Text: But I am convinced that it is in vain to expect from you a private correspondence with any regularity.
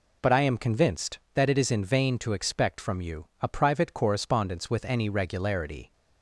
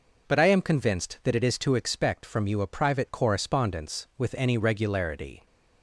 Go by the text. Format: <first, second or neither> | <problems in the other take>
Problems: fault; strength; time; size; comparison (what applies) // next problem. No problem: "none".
first | skips "in vain"; at 1.5 s